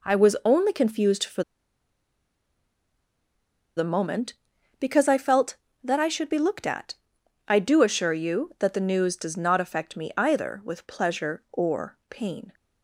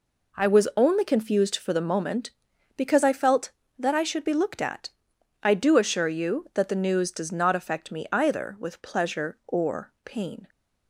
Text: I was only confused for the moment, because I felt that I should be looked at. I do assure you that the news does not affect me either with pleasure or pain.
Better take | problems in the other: second | pauses between "for" and "the"; strong; at 1.4 s; 2.3 s long

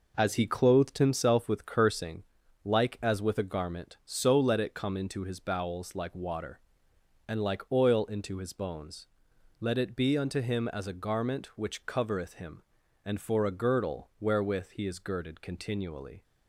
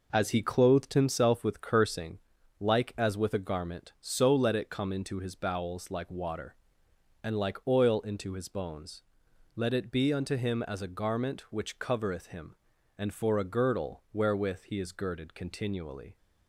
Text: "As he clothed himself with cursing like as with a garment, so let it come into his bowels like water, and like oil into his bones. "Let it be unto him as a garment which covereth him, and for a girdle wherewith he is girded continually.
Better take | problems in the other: neither | pauses between "cursing" and "like"; the same in both

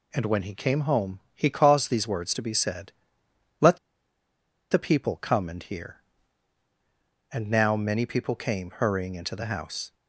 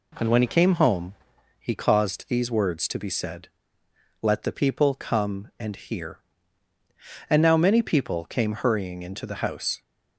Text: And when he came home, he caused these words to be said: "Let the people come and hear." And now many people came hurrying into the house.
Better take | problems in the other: second | pauses between "Let" and "the"; noticeable; at 3.7 s; 0.94 s long

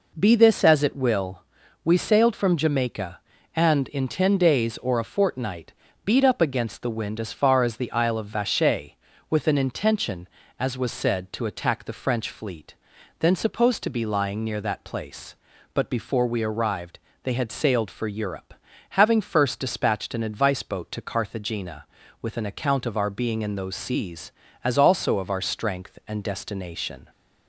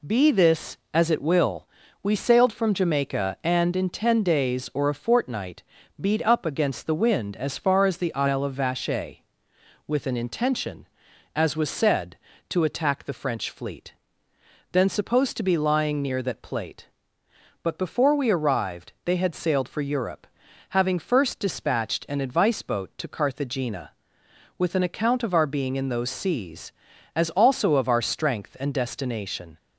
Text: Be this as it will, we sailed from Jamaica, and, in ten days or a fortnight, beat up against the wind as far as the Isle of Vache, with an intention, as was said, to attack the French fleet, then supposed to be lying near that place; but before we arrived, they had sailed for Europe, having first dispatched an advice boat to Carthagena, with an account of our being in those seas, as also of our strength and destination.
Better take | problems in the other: first | says "plate" for "place"; at 16.4 s

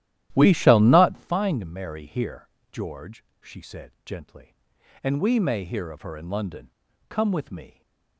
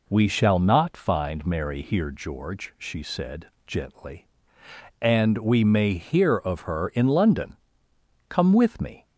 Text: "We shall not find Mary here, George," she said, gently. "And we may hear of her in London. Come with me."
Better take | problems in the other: second | starts louder than the rest; strong; until 1.4 s; 12.5 dB

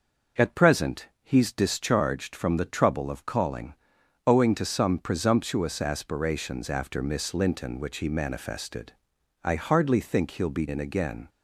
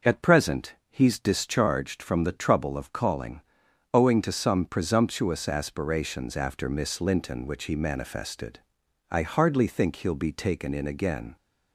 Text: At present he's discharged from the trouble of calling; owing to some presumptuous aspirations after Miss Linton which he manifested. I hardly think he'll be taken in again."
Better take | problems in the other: second | skips "taken"; at 10.6 s

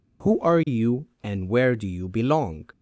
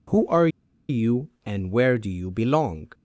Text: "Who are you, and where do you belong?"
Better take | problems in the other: first | pauses between "are" and "you"; at 0.4 s; 0.40 s long

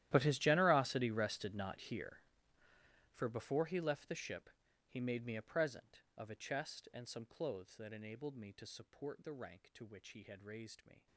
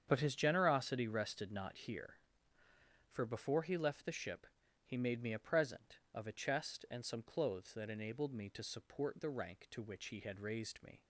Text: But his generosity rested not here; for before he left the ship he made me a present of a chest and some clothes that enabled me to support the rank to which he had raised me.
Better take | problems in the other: second | gets quieter; strong; throughout; 21.5 dB // starts louder than the rest; strong; until 1.1 s; 13 dB; strong in the second // pauses between "ship" and "he"; slight; at 4.5 s; 0.36 s long; slight in the second

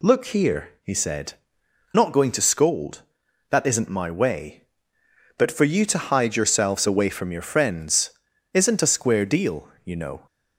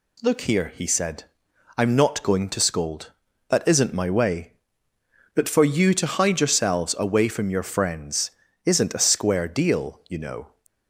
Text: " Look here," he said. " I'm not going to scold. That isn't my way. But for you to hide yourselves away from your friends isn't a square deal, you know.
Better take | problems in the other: second | skips "I'm"; at 1.9 s // pauses between "friends" and "isn't"; at 8.0 s; 0.42 s long; slight in the second

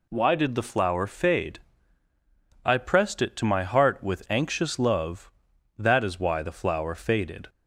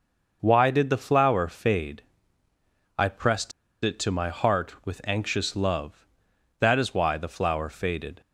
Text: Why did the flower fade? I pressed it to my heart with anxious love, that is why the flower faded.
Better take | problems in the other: first | pauses between "pressed" and "it"; slight; at 3.5 s; 0.33 s long

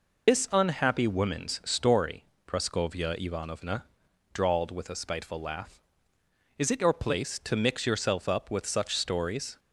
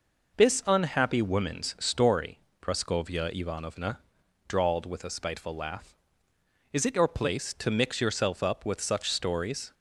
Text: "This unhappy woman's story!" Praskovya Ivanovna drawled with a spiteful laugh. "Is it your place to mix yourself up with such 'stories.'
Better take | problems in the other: second | loses the start of "This"; at 0.2 s; 70 ms // pauses between "Ivanovna" and "drawled"; noticeable; at 3.8 s; 0.48 s long; noticeable in the second

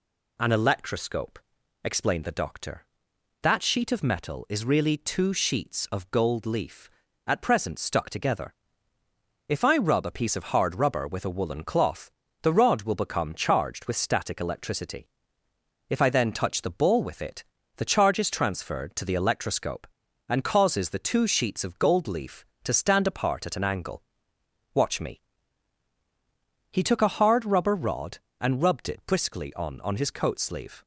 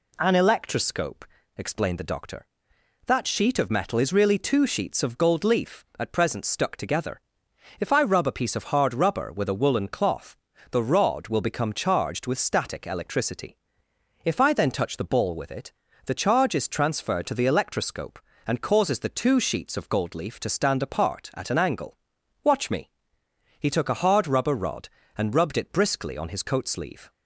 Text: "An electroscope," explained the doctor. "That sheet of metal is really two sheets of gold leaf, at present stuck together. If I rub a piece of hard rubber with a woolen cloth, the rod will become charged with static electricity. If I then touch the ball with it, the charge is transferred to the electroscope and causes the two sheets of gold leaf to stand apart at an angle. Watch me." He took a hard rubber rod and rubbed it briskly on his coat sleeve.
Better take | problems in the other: second | says "on" twice; at 29.8 s

